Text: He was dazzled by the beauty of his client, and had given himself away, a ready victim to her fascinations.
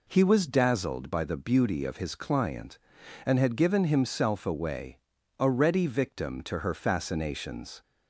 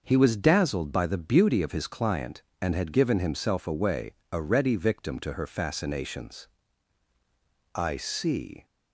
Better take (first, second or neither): first